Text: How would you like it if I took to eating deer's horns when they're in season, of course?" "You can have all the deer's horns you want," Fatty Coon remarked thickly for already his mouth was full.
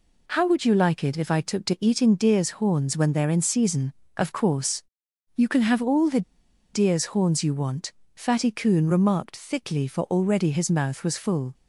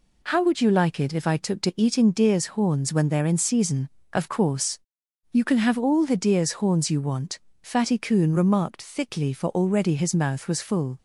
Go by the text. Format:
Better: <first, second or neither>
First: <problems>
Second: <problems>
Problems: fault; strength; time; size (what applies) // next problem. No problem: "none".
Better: second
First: pauses between "the" and "deer's"; noticeable; at 6.2 s; 0.51 s long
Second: none